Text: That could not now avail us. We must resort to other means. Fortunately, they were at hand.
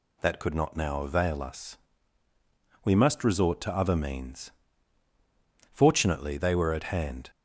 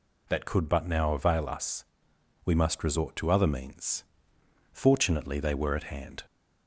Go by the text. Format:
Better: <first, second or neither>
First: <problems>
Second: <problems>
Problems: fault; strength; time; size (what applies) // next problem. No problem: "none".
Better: first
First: none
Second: says "but" for "not"; at 0.6 s